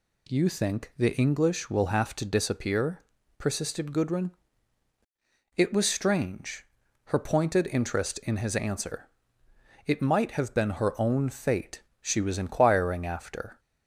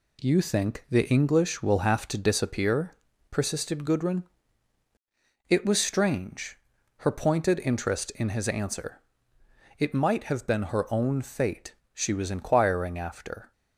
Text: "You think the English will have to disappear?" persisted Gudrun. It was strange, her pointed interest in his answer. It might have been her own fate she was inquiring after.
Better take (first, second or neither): first